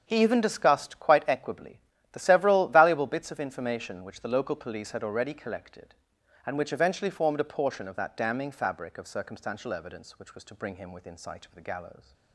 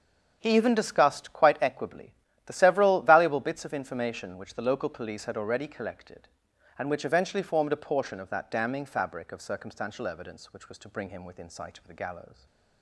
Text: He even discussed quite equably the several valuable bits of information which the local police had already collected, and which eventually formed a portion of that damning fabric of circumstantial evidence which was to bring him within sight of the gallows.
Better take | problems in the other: neither | starts louder than the rest; the same in both // pauses between "equably" and "the"; slight; the same in both

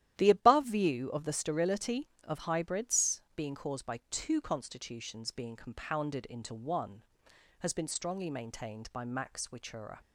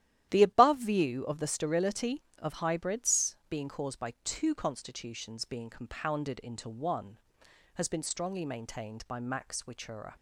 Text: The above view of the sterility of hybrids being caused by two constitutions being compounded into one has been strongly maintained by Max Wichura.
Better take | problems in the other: neither | starts louder than the rest; strong; the same in both

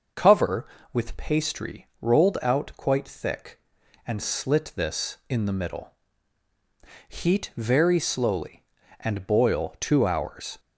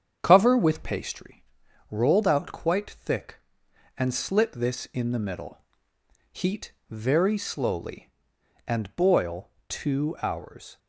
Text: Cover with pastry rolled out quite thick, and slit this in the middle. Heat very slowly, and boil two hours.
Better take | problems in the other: first | starts louder than the rest; strong; until 1.2 s; 8 dB // pauses between "pastry" and "rolled"; noticeable; at 1.4 s; 0.46 s long // pauses between "Heat" and "very"; slight; at 6.7 s; 0.18 s long // pauses between "boil" and "two"; slight; at 9.4 s; 0.22 s long

